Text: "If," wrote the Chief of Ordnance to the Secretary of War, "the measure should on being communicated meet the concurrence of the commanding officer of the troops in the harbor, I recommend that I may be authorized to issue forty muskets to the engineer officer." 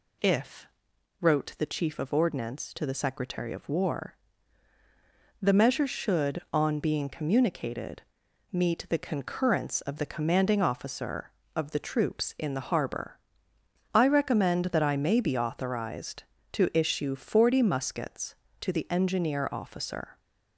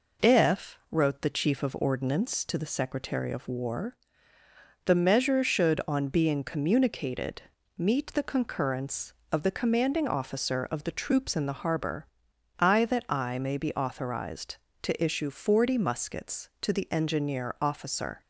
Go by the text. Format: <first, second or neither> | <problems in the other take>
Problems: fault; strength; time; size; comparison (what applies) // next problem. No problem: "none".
first | pauses between "communicated" and "meet"; at 7.4 s; 0.38 s long; noticeable in the first // skips "recommend"; at 12.8 s